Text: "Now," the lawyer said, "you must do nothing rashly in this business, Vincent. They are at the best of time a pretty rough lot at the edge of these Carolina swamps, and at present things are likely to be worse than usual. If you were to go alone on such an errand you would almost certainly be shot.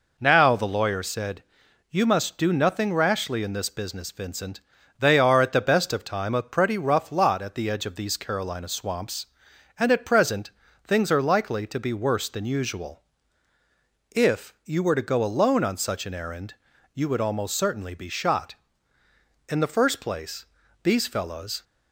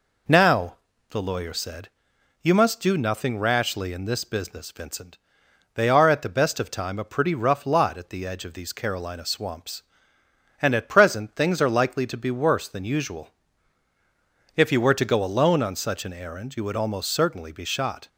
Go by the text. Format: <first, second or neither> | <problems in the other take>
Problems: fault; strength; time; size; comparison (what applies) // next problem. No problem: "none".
second | pauses between "present" and "things"; slight; at 10.5 s; 0.34 s long // pauses between "errand" and "you"; at 16.5 s; 0.44 s long // goes on to say "In the first place these fellows"; strong; from 19.4 s on; 2.1 s long